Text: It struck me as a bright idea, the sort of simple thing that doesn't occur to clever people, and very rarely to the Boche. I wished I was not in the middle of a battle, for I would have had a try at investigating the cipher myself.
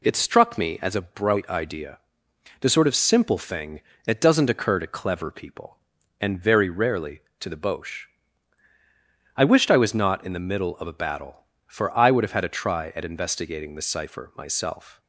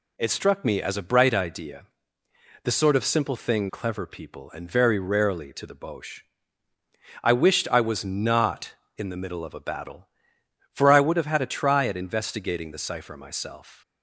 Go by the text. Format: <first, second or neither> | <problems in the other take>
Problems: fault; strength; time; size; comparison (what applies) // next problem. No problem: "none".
first | skips "that doesn't occur to"; at 3.6 s